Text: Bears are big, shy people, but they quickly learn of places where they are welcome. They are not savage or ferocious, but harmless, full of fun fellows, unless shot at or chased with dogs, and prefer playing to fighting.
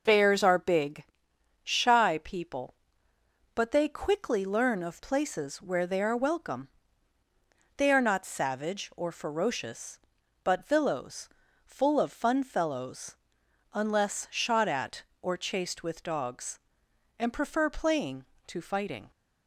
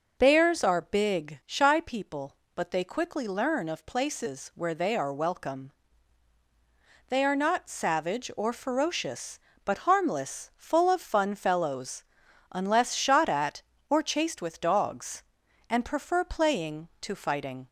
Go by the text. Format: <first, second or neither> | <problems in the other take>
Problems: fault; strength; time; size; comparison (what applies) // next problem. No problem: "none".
second | says "villows" for "harmless"; at 10.6 s